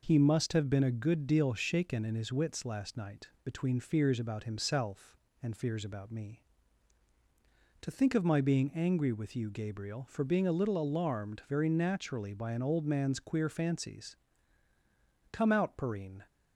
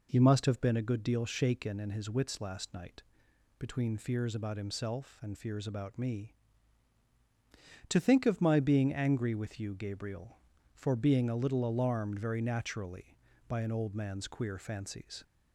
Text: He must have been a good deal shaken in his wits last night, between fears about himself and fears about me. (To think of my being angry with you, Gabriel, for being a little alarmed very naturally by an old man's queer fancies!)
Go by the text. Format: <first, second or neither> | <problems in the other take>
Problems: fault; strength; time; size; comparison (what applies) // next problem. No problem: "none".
second | goes on to say "Come out Perrine"; noticeable; from 15.3 s on; 0.92 s long